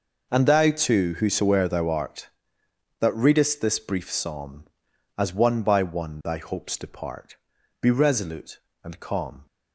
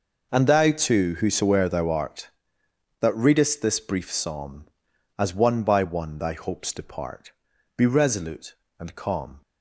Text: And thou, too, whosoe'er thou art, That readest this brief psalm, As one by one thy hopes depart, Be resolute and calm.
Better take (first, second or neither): neither